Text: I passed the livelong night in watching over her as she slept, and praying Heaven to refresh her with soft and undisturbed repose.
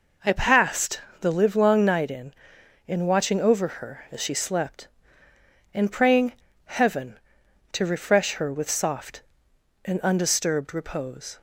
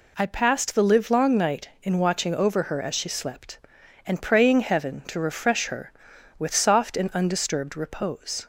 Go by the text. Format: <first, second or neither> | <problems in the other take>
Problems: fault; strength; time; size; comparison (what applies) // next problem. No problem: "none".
second | pauses between "passed" and "the"; slight; at 0.9 s; 0.22 s long // says "in" twice; at 2.8 s // pauses between "praying" and "Heaven"; slight; at 6.3 s; 0.32 s long